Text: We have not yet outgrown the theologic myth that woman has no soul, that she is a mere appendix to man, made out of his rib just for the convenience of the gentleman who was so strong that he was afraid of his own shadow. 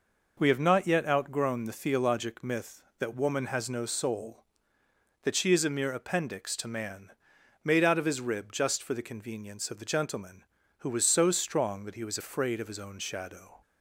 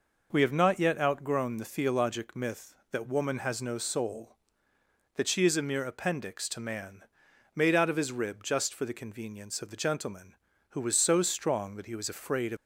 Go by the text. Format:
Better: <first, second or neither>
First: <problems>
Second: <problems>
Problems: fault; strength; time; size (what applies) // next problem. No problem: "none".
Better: first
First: none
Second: stops before "his own shadow"; at 12.5 s